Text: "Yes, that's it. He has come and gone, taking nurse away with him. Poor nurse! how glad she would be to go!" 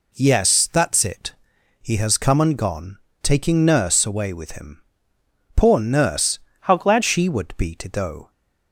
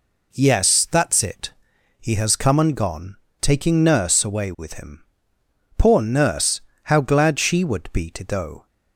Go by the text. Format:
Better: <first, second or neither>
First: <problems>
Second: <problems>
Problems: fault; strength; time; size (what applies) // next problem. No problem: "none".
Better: second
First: changes voice from "how" to "glad"; from 6.6 to 7.0 s; 0.4 s long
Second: none